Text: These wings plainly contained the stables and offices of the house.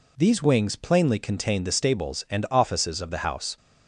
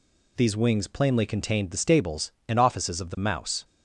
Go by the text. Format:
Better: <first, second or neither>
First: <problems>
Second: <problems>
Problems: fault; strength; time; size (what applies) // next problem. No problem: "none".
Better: first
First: none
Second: says "mouse" for "house"; at 3.1 s